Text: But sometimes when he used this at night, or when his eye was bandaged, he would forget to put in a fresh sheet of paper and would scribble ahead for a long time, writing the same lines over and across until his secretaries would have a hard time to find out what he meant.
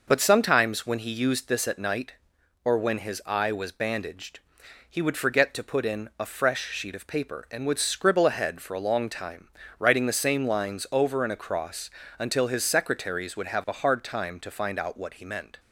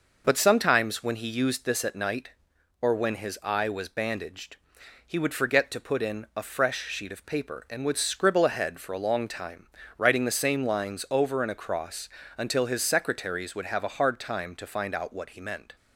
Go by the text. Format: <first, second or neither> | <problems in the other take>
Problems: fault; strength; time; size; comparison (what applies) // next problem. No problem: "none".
neither | pauses between "across" and "until"; slight; the same in both